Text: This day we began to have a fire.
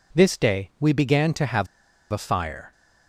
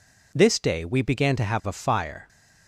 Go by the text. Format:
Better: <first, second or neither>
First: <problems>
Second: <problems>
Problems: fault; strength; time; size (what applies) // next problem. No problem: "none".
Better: second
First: pauses between "have" and "a"; noticeable; at 1.6 s; 0.46 s long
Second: none